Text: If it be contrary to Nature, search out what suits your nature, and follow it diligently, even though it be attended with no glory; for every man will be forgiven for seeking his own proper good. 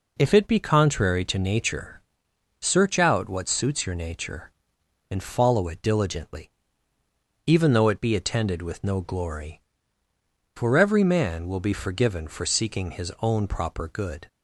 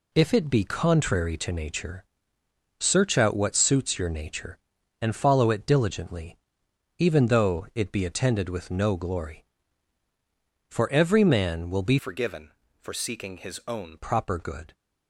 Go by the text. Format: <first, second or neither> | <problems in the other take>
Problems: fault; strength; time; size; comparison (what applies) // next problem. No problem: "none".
first | changes voice from "forgiven" to "own"; from 11.9 to 13.9 s; 2.0 s long